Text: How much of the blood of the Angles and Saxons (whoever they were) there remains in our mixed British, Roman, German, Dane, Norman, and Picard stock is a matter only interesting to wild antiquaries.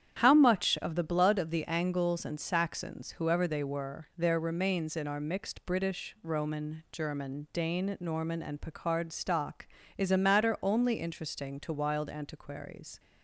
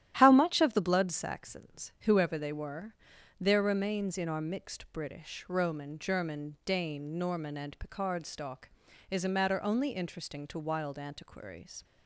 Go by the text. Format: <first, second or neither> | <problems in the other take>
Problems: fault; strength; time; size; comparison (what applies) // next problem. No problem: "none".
first | starts louder than the rest; strong; until 1.2 s; 12 dB; strong in the first // skips "of the Angles and"; at 1.1 s